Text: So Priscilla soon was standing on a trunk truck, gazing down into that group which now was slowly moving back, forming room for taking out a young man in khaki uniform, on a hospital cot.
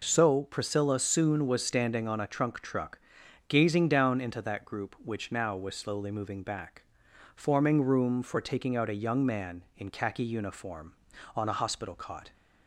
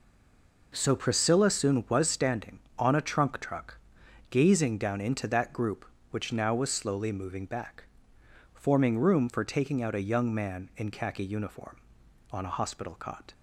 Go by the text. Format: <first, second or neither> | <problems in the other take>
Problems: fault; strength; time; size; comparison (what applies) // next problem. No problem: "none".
first | stays silent before the first word; slight; until 0.7 s; 0.7 s long